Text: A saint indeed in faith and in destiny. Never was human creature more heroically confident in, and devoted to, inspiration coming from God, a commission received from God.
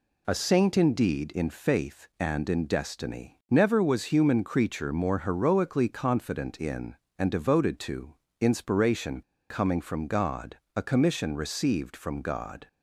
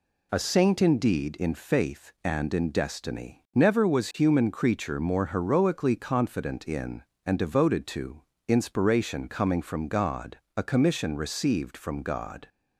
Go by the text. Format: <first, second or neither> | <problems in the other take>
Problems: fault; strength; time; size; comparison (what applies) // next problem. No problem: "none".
second | pauses between "inspiration" and "coming"; slight; at 9.2 s; 0.29 s long